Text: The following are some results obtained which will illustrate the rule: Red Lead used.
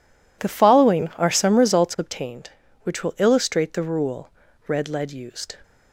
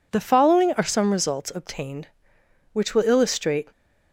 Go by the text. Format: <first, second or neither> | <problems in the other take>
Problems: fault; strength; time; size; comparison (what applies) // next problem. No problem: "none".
first | stops before "the rule Red Lead used"; at 3.7 s